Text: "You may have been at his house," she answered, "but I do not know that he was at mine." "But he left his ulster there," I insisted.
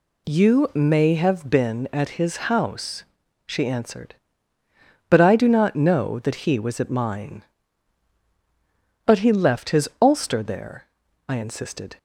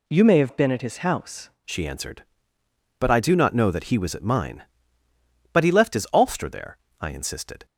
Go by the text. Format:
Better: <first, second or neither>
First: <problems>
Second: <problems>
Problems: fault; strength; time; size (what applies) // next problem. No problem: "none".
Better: first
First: none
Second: changes voice at "she"; from 1.6 s on; 6.0 s long